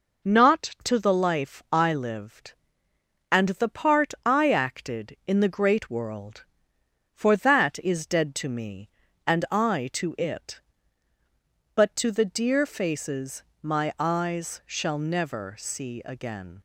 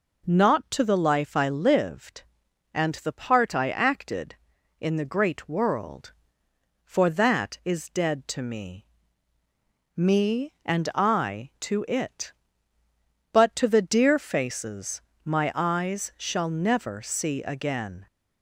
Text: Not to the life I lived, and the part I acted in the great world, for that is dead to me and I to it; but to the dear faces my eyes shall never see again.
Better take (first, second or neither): first